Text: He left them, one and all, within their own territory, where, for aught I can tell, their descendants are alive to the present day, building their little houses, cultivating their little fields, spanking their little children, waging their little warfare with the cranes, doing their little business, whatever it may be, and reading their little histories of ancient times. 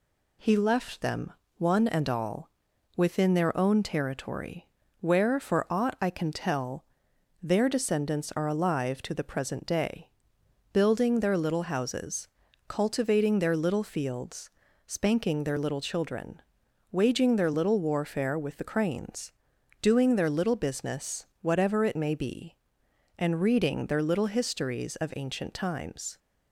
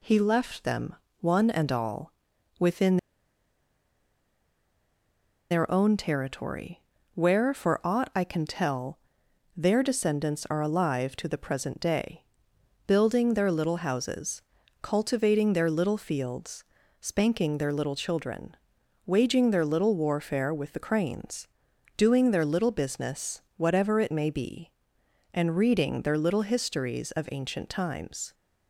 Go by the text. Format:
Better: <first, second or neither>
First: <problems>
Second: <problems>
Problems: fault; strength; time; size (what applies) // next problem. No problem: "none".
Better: first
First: none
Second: pauses between "within" and "their"; strong; at 2.9 s; 2.5 s long